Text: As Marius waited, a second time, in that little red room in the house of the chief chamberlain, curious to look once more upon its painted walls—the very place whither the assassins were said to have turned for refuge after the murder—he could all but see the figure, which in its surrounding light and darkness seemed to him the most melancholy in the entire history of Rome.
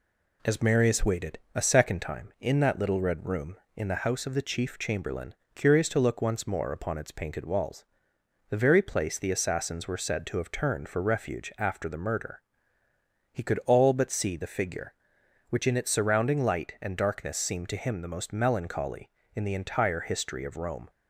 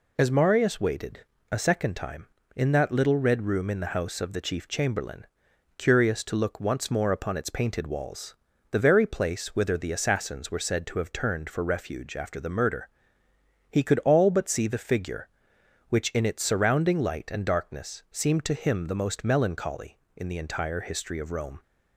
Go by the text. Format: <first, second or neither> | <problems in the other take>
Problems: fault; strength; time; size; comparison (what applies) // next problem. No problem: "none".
second | skips "whither"; at 9.1 s